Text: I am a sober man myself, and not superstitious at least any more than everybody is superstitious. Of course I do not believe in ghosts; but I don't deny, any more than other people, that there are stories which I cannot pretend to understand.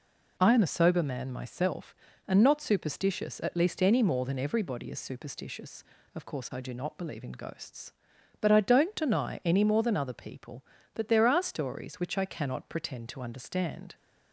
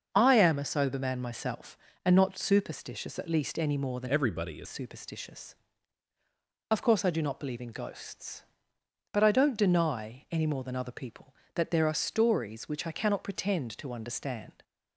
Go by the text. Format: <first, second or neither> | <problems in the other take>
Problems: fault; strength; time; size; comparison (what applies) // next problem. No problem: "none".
first | starts louder than the rest; until 1.1 s; 6.5 dB // changes voice from "everybody" to "is"; from 4.0 to 4.6 s; 0.6 s long